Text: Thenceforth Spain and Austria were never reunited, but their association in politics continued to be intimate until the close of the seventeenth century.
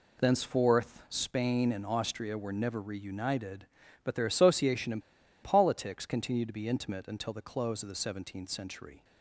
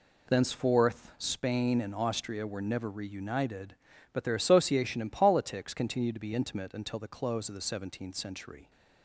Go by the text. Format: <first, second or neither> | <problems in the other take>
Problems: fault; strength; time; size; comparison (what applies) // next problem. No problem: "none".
second | pauses between "in" and "politics"; at 5.0 s; 0.41 s long